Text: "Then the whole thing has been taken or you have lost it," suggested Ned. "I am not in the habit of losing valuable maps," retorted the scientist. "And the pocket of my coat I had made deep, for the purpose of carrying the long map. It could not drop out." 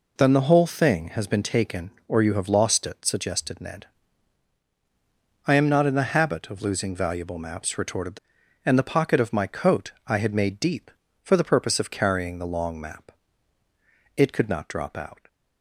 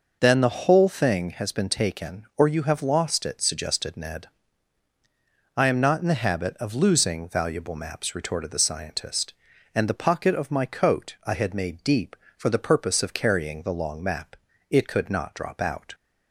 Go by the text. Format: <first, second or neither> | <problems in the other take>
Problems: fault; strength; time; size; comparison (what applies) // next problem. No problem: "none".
second | skips "scientist"; at 8.4 s